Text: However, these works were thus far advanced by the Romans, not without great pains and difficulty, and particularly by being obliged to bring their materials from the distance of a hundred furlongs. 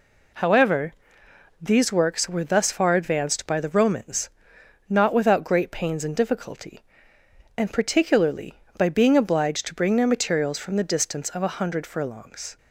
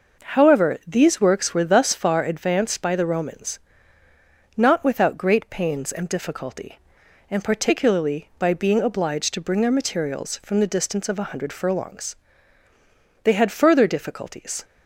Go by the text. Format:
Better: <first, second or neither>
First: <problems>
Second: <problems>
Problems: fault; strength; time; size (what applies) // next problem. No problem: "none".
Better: first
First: none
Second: goes on to say "They had further difficulties"; from 13.2 s on; 1.4 s long